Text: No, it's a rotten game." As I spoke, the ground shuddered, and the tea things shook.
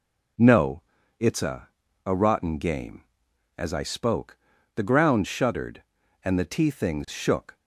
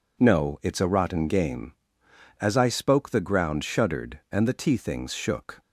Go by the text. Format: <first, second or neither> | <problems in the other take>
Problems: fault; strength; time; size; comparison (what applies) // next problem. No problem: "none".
second | says "a" twice; at 2.0 s